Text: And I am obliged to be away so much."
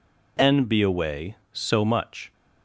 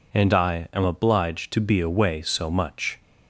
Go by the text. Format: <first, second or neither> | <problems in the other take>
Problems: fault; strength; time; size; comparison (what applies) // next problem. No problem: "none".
second | skips "I am obliged to"; at 0.6 s